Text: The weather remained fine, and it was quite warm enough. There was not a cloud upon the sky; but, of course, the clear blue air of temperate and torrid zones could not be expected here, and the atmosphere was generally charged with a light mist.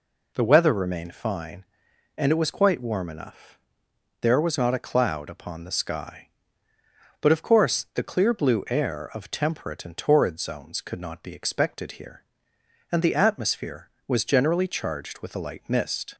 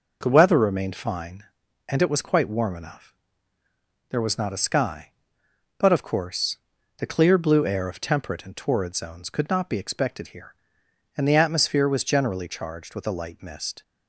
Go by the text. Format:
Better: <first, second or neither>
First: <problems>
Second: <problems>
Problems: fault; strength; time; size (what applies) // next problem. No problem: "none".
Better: first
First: none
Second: skips "cloud upon the"; at 4.6 s